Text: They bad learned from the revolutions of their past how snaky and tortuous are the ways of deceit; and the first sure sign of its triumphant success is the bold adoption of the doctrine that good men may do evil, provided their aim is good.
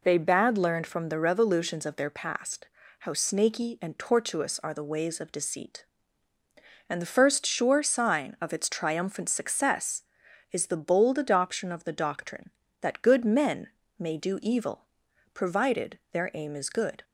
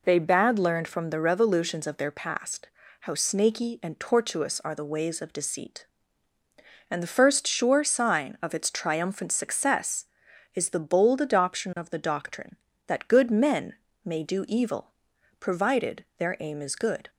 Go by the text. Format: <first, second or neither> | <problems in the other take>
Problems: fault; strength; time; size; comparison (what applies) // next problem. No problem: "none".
neither | pauses between "past" and "how"; slight; the same in both // pauses between "men" and "may"; slight; the same in both